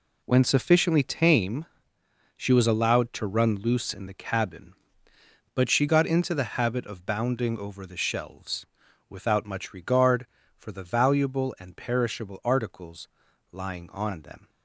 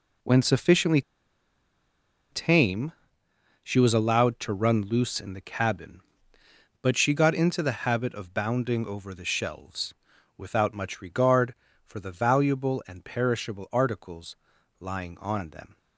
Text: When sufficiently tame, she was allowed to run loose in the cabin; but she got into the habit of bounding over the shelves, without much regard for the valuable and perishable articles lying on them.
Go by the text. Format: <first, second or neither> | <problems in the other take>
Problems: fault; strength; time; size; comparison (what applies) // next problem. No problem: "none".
first | pauses between "sufficiently" and "tame"; strong; at 1.0 s; 1.3 s long // pauses between "articles" and "lying"; at 14.3 s; 0.44 s long; also in the first